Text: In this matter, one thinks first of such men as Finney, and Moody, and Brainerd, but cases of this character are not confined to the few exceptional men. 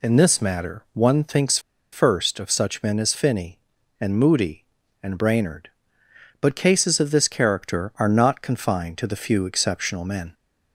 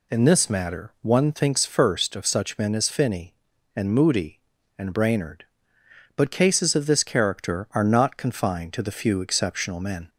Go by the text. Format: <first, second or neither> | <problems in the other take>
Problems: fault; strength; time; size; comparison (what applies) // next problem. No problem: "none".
second | pauses between "thinks" and "first"; slight; at 1.5 s; 0.33 s long